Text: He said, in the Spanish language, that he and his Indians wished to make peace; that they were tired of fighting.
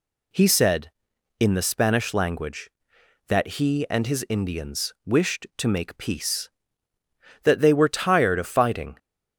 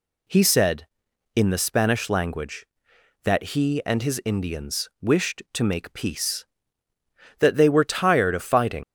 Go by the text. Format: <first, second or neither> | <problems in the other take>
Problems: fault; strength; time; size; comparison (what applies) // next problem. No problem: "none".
first | leaves "fighting" unfinished; at 8.8 s; 105 ms